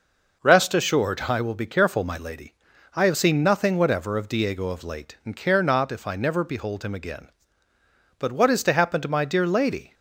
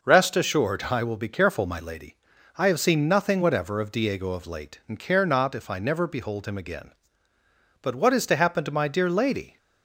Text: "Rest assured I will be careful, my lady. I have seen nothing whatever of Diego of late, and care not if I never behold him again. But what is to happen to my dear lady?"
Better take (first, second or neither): neither